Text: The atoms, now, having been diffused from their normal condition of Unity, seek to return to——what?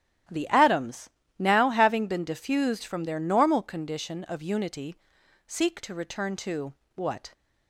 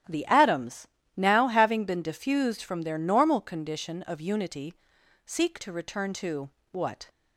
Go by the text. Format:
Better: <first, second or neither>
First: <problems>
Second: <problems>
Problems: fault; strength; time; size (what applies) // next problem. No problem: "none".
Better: neither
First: starts louder than the rest; strong; until 1.6 s; 12 dB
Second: starts louder than the rest; strong; until 1.4 s; 12.5 dB